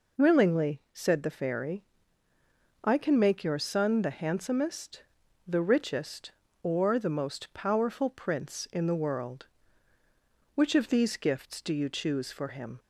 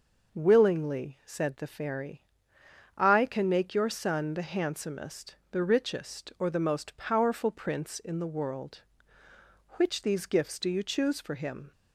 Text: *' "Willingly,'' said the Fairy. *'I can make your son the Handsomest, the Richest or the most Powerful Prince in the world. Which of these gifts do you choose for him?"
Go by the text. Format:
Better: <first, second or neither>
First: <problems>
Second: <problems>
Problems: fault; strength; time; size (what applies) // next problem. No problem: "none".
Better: first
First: none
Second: skips "of"; at 10.0 s